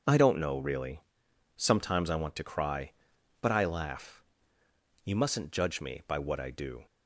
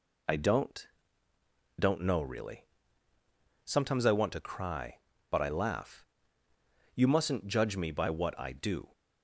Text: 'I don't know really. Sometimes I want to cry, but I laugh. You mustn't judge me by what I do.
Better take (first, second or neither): first